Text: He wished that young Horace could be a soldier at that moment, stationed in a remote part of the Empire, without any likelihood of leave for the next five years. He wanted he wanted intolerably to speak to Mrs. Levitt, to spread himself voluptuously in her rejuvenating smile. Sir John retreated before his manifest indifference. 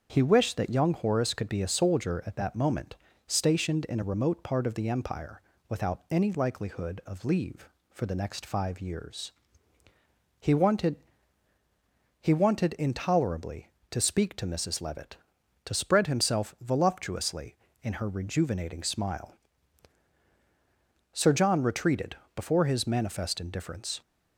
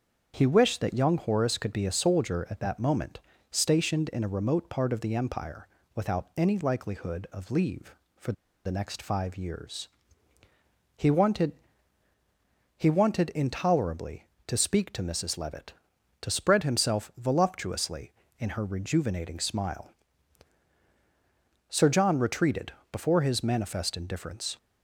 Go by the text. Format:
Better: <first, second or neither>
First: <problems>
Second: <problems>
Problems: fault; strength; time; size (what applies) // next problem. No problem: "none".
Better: first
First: starts louder than the rest; strong; until 1.1 s; 7 dB // pauses between "wanted" and "he"; strong; at 10.9 s; 1.2 s long // pauses between "retreated" and "before"; slight; at 22.1 s; 0.20 s long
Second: starts louder than the rest; strong; until 1.3 s; 7 dB // pauses between "for" and "the"; slight; at 8.3 s; 0.32 s long // pauses between "wanted" and "he"; strong; at 11.5 s; 1.2 s long // pauses between "retreated" and "before"; slight; at 22.7 s; 0.20 s long